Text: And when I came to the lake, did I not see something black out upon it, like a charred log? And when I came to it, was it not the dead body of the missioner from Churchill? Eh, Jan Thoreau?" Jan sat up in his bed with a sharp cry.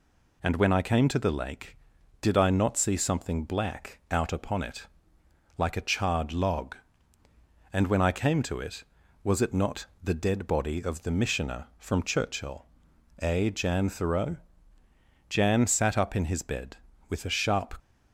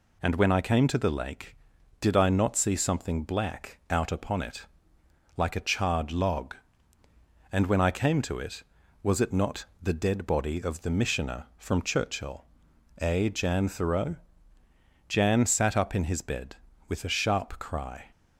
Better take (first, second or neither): second